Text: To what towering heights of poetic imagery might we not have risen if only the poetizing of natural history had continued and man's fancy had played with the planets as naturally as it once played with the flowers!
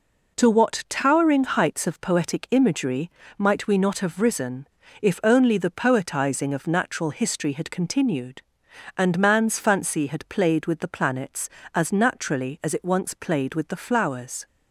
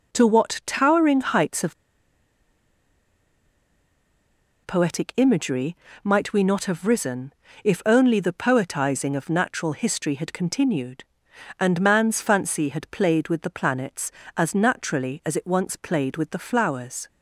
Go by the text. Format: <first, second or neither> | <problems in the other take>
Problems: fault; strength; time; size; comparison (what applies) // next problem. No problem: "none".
first | pauses between "of" and "poetic"; strong; at 1.7 s; 2.9 s long // pauses between "imagery" and "might"; slight; at 5.7 s; 0.28 s long; slight in the first // pauses between "risen" and "if"; slight; at 7.3 s; 0.32 s long; slight in the first